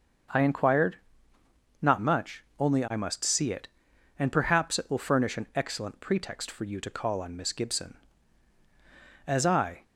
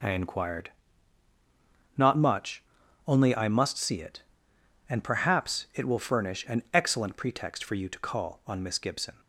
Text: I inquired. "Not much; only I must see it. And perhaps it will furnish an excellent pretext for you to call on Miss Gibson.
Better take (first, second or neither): second